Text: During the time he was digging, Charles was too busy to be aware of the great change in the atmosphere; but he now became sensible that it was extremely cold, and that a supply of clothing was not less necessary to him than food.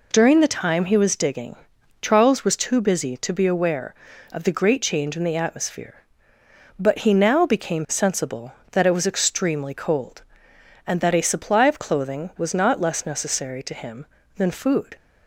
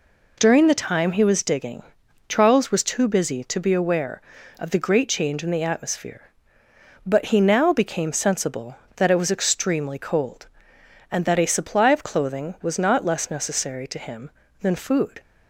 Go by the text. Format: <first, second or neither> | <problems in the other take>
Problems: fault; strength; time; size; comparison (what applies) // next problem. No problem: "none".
neither | none